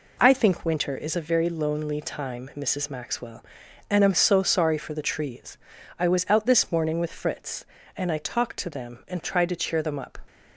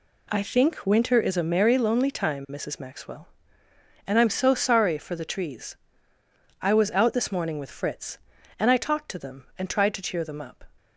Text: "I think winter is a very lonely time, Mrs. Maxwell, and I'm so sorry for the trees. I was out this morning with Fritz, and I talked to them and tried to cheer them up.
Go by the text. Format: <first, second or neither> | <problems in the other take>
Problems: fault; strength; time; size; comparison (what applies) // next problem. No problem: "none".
first | says "merry" for "very"; at 1.5 s